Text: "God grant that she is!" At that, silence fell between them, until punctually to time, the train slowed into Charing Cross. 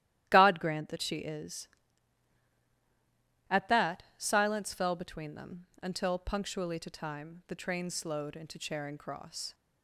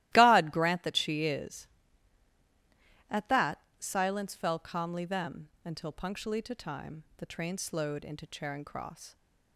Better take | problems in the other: first | starts louder than the rest; strong; until 1.1 s; 15.5 dB; strong in the first // says "calmly" for "between"; at 4.5 s

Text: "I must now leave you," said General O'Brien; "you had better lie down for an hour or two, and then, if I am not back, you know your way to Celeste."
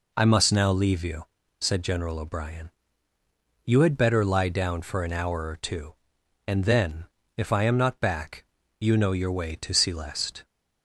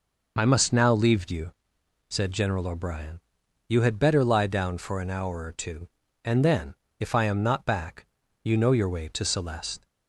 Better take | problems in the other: neither | none

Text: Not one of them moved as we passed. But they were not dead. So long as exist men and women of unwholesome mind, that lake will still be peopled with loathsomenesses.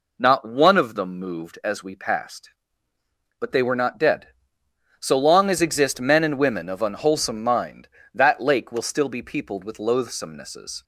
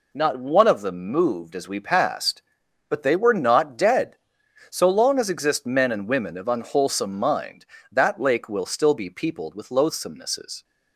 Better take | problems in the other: neither | none

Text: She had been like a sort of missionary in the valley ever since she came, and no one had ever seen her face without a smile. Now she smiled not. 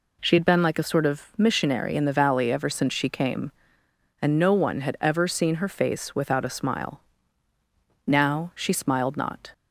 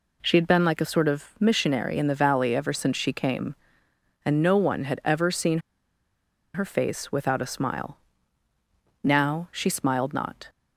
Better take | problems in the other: first | pauses between "seen" and "her"; noticeable; at 5.5 s; 0.95 s long

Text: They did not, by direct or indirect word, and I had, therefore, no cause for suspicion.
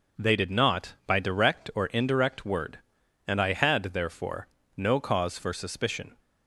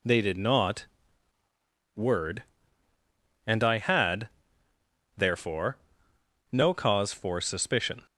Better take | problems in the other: first | skips "by direct or indirect"; at 1.4 s

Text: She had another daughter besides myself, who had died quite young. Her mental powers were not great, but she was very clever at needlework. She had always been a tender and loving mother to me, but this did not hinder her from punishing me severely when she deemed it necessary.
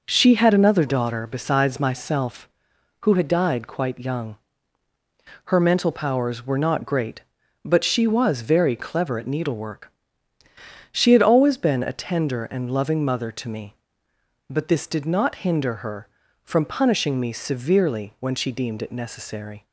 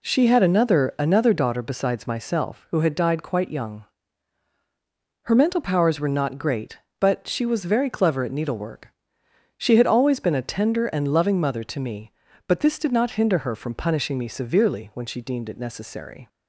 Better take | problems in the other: first | says "another" twice; at 0.9 s

